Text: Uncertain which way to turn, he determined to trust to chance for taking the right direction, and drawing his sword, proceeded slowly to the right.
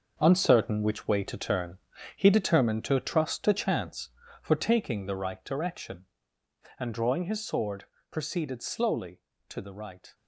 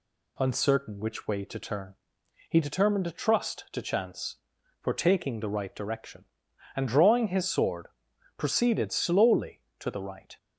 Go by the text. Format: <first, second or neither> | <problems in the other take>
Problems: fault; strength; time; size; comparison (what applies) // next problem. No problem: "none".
second | gets quieter; strong; throughout; 10 dB